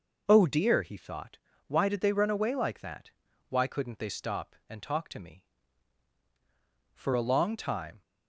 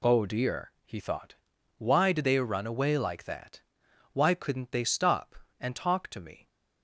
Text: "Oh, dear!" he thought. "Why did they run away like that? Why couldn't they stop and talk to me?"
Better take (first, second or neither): second